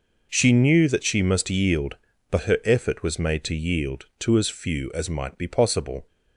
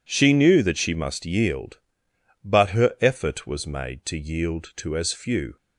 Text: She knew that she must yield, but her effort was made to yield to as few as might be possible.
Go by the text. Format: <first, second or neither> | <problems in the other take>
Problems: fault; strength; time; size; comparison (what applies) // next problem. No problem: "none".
first | stops before "as might be possible"; at 5.5 s